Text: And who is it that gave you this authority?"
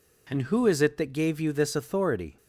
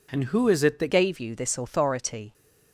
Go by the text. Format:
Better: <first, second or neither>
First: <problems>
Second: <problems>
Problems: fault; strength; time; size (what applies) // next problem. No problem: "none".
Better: first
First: none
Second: changes voice at "gave"; from 0.8 s on; 1.5 s long